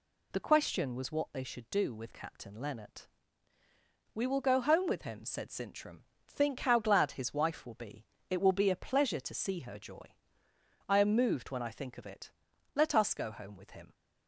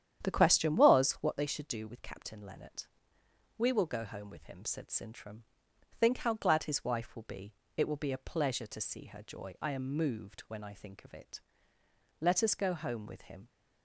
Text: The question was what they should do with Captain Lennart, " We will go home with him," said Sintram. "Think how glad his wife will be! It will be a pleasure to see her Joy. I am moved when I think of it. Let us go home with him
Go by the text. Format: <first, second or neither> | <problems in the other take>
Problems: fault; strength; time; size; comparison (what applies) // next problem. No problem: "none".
first | starts louder than the rest; strong; until 1.5 s; 9.5 dB